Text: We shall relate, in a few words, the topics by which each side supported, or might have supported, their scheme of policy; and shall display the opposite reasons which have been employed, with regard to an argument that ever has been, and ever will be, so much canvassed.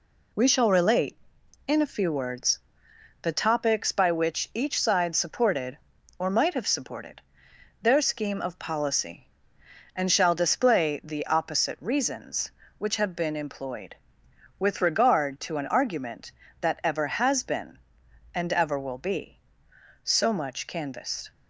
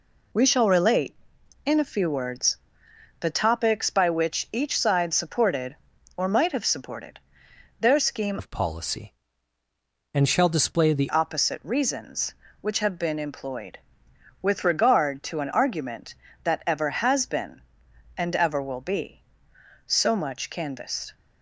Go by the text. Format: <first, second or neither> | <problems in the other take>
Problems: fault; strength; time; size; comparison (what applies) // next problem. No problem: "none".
first | changes voice from "of" to "the"; from 8.3 to 11.0 s; 2.7 s long